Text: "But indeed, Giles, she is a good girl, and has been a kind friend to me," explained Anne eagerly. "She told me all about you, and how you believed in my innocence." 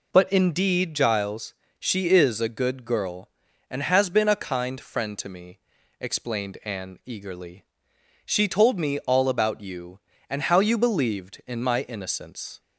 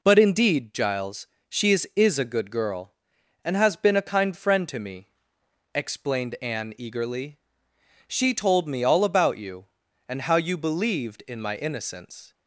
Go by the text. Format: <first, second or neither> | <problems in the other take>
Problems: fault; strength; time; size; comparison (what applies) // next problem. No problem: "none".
first | says "is" twice; at 1.9 s